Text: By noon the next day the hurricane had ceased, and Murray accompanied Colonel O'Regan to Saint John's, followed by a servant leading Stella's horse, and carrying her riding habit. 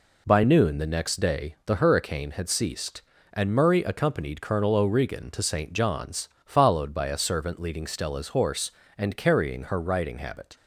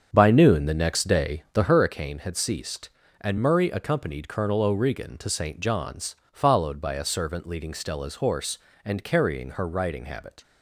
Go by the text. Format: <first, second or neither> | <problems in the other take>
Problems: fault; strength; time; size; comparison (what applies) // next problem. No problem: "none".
first | starts louder than the rest; strong; until 1.9 s; 7.5 dB